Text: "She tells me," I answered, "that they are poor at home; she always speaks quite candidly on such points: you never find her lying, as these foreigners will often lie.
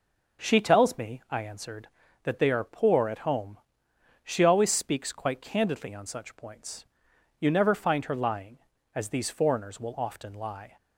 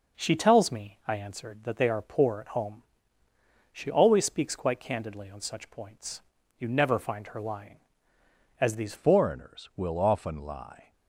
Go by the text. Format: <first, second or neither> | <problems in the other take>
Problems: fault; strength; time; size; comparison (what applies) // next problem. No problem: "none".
first | changes voice at "foreigners"; from 8.9 s on; 2.0 s long